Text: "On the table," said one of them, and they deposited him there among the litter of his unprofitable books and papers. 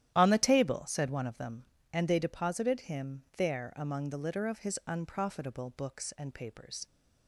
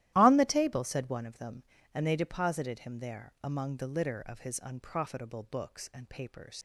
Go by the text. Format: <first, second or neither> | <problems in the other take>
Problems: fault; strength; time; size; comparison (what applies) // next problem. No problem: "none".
first | starts louder than the rest; strong; until 1.1 s; 14 dB; strong in the first // leaves "papers" unfinished; at 6.5 s; 75 ms